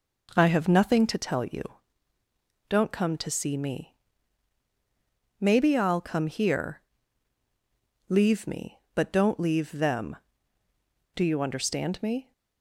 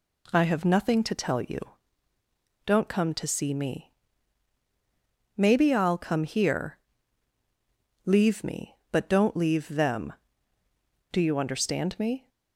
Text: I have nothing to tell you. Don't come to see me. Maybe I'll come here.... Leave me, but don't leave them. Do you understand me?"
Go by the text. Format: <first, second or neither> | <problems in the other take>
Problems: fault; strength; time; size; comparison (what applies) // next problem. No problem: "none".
second | starts louder than the rest; noticeable; until 1.2 s; 5 dB